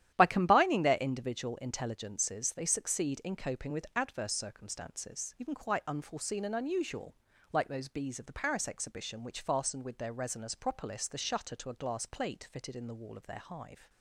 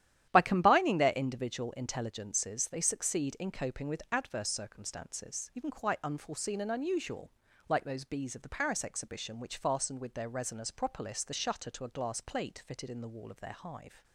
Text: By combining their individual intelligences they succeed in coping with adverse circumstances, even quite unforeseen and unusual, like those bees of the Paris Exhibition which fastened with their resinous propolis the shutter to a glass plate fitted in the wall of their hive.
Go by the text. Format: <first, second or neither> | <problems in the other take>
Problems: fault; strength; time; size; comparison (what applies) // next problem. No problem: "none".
neither | starts louder than the rest; strong; the same in both